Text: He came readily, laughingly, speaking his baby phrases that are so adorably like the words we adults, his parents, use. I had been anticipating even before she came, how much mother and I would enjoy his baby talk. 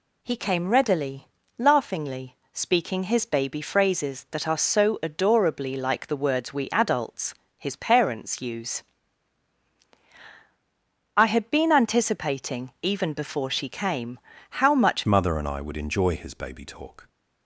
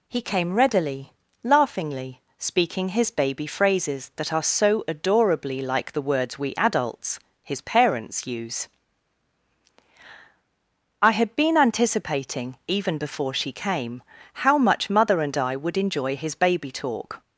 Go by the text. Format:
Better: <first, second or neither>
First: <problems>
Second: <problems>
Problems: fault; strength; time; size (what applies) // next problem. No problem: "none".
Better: second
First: changes voice at "mother"; from 15.0 s on; 2.0 s long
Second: none